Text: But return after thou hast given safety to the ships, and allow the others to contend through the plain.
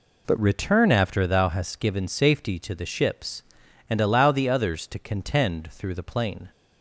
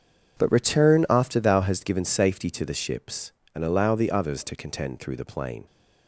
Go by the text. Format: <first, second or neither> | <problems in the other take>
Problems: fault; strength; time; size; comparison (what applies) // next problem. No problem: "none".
second | changes voice at "return"; from 0.3 s on; 6.2 s long